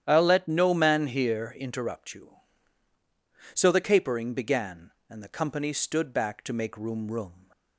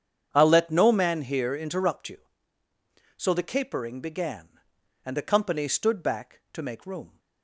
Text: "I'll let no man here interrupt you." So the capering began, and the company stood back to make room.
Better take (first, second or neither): second